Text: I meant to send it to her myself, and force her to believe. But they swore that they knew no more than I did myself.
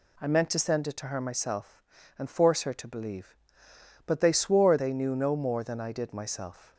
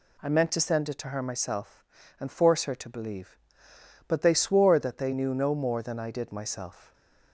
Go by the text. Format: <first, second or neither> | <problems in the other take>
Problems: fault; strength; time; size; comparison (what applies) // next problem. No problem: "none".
second | skips "that"; at 4.7 s